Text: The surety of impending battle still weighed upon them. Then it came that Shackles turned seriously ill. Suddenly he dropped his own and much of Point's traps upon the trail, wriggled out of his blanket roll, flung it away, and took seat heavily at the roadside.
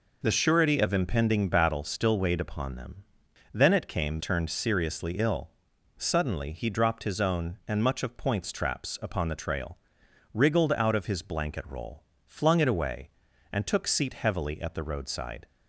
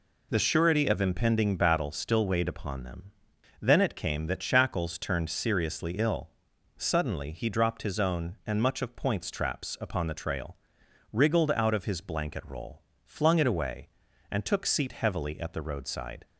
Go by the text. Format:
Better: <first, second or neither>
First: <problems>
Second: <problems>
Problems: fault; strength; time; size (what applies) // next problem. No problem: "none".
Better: second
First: skips "that Shackles"; at 4.1 s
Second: none